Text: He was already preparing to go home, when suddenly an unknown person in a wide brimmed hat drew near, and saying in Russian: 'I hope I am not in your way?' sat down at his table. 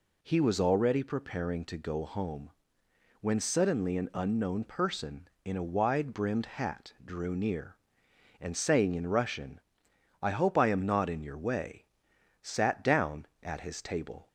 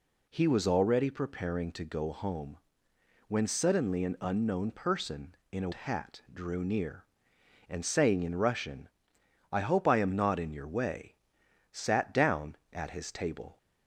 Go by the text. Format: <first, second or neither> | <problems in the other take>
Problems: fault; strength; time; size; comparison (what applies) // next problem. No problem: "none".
first | skips "wide brimmed"; at 5.7 s